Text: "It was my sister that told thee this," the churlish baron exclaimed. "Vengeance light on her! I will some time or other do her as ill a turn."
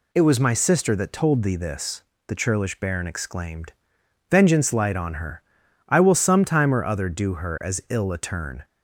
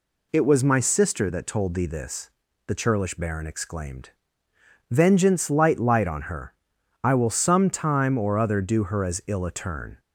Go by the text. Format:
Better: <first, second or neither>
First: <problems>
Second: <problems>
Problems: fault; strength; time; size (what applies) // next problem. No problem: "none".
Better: first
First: none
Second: says "light" twice; at 5.7 s